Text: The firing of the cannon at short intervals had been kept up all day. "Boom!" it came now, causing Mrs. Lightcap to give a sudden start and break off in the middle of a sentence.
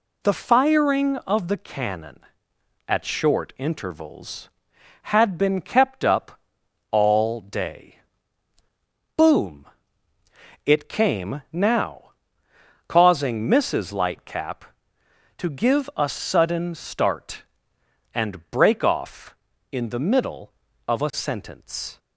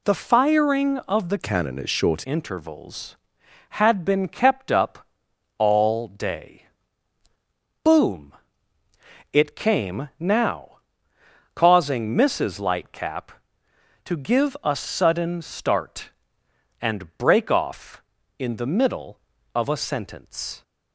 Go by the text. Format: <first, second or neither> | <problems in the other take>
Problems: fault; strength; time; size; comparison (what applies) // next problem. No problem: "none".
first | changes voice from "cannon" to "short"; from 1.3 to 2.2 s; 0.9 s long // pauses between "up" and "all"; noticeable; at 5.0 s; 0.54 s long; noticeable in the first